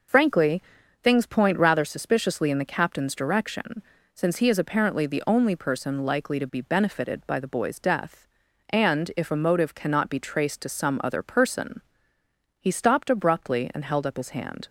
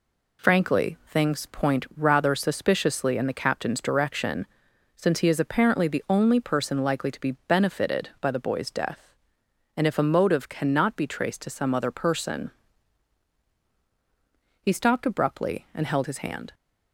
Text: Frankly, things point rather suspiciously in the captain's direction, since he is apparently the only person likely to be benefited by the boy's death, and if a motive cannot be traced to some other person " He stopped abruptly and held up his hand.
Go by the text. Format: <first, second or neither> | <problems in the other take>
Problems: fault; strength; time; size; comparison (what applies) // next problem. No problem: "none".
first | skips "up"; at 16.0 s